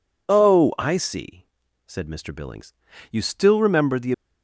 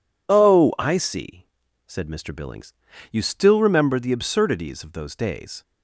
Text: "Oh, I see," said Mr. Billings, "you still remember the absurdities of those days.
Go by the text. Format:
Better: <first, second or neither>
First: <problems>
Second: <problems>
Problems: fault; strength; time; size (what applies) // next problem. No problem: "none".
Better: second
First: stops before "absurdities of those days"; at 4.1 s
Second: none